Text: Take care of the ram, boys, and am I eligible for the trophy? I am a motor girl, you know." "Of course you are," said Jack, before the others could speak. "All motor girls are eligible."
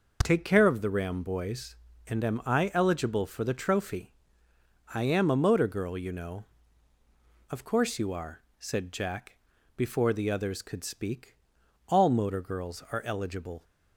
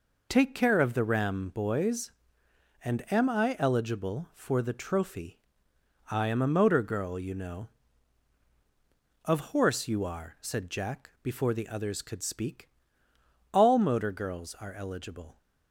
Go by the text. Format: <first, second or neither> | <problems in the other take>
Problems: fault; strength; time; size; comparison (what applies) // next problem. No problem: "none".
first | says "horse" for "course"; at 9.5 s